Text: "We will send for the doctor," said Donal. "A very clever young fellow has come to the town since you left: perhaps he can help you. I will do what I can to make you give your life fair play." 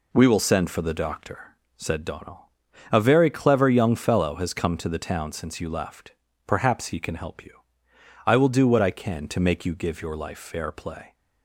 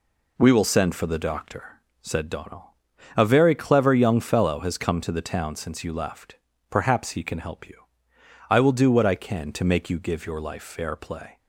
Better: neither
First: none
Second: none

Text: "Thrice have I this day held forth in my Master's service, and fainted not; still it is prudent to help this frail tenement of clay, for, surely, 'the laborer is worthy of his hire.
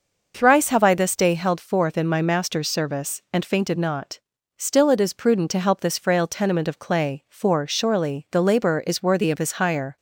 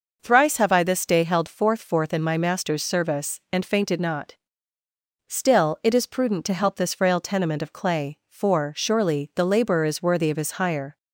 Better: first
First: none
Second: says "forth" twice; at 1.7 s

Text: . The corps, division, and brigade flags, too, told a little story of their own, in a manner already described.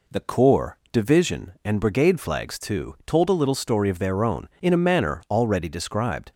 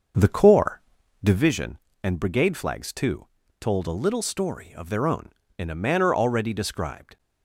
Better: first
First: none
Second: starts louder than the rest; until 1.5 s; 6 dB

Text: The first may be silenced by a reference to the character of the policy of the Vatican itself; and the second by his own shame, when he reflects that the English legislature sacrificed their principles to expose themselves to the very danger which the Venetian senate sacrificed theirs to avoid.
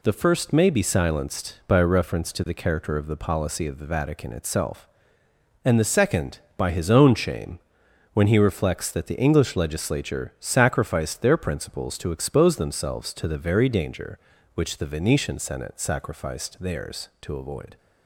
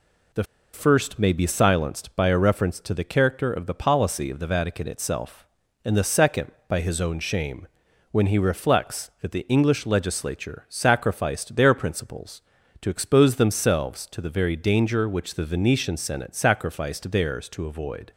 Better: first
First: none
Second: pauses between "The" and "first"; slight; at 0.4 s; 0.29 s long

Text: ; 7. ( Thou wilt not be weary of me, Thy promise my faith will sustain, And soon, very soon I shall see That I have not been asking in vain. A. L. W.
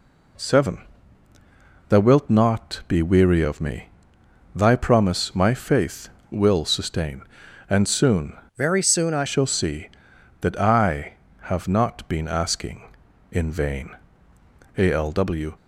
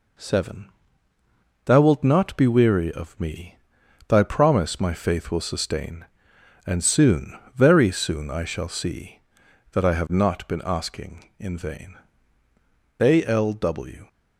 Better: second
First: changes voice from "very" to "I"; from 8.5 to 9.2 s; 0.7 s long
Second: none

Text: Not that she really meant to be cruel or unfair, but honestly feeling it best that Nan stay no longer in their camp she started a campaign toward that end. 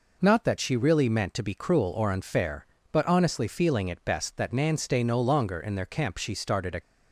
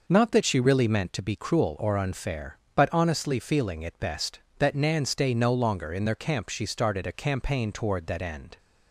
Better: second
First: stops before "campaign toward that end"; at 6.8 s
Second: none

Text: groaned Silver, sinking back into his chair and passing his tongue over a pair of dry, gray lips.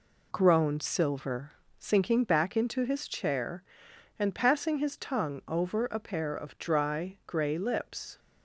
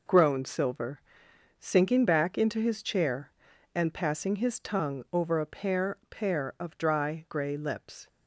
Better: first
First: none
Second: says "pair" twice; at 6.0 s

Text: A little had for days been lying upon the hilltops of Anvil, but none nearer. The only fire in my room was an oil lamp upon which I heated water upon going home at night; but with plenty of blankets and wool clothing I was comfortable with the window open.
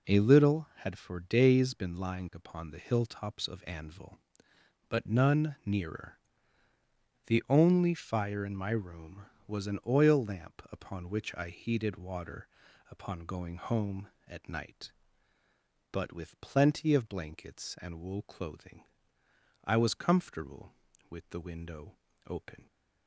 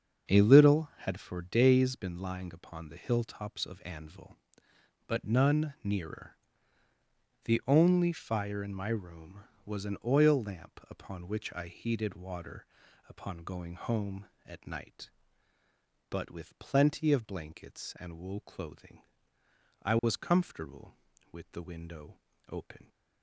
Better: first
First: pauses between "water" and "upon"; at 12.4 s; 0.44 s long // pauses between "clothing" and "I"; noticeable; at 18.8 s; 0.80 s long // pauses between "window" and "open"; slight; at 21.9 s; 0.30 s long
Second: starts louder than the rest; until 1.6 s; 7 dB // pauses between "water" and "upon"; at 12.6 s; 0.44 s long // pauses between "clothing" and "I"; noticeable; at 19.0 s; 0.80 s long // pauses between "window" and "open"; slight; at 22.1 s; 0.30 s long

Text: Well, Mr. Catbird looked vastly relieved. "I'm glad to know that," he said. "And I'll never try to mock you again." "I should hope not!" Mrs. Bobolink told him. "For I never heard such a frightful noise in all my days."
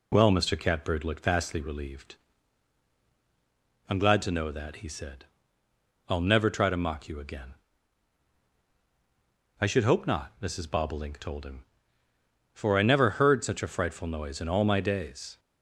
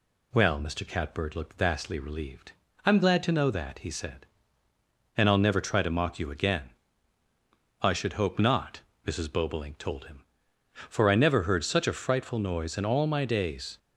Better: second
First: skips "And"; at 5.6 s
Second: none

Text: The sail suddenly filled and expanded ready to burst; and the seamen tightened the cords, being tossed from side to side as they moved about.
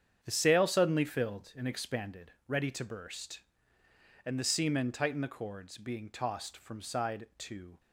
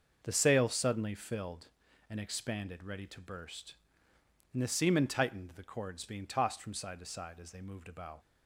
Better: second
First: starts louder than the rest; strong; until 1.2 s; 8 dB // stops before "side as they moved about"; at 7.7 s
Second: starts louder than the rest; until 1.2 s; 6.5 dB

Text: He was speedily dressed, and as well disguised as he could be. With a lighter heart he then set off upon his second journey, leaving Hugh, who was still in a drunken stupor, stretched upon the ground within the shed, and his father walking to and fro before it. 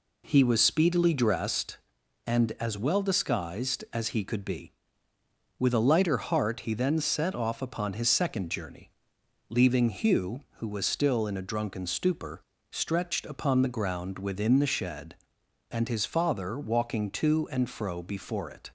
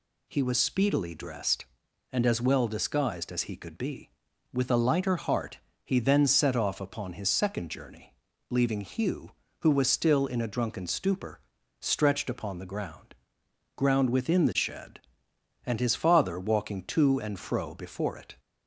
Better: first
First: none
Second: pauses between "heart" and "he"; slight; at 5.5 s; 0.26 s long // says "ground" twice; at 13.7 s

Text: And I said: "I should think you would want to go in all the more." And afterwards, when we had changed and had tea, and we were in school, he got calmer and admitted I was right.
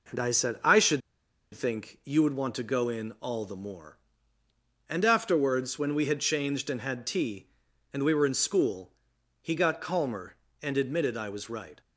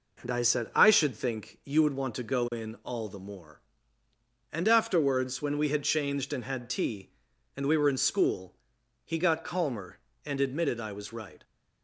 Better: second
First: pauses between "should" and "think"; noticeable; at 1.0 s; 0.53 s long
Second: none

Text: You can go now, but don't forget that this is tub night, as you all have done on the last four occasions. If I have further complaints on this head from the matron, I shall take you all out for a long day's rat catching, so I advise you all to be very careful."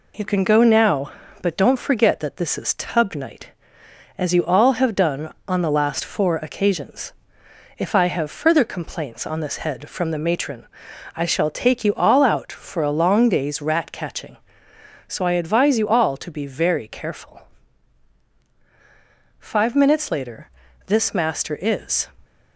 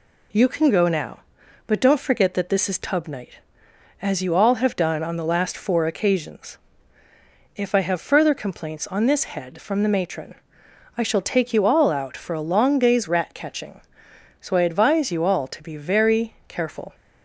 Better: second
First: goes on to say "Five minutes later this master is"; strong; from 19.3 s on; 2.7 s long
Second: none

